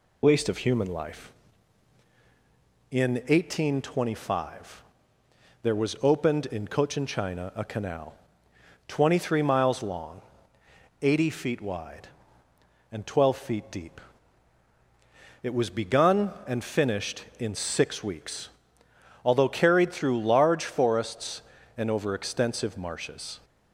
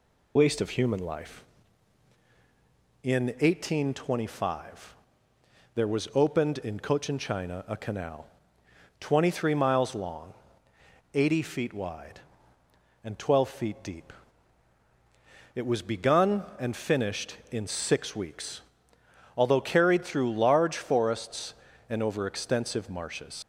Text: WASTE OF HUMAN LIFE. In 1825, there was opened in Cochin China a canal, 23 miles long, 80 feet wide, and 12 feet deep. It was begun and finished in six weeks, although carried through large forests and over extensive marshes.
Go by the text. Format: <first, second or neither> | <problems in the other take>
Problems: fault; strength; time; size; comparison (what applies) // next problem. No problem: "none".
first | leaves "marshes" unfinished; at 23.4 s; 140 ms